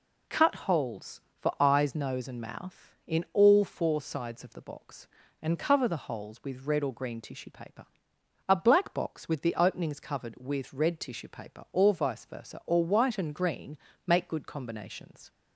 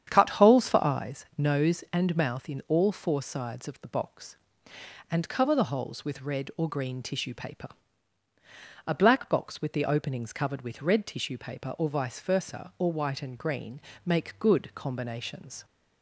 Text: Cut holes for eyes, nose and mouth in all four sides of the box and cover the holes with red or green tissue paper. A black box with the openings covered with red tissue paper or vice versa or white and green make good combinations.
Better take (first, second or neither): first